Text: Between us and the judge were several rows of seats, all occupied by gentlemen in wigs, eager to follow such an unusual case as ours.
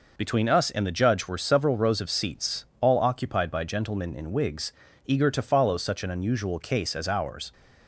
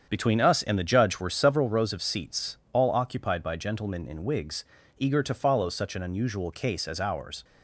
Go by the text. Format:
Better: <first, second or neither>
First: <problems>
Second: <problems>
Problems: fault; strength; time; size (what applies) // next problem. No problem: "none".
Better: first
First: none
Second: starts louder than the rest; strong; until 1.8 s; 7.5 dB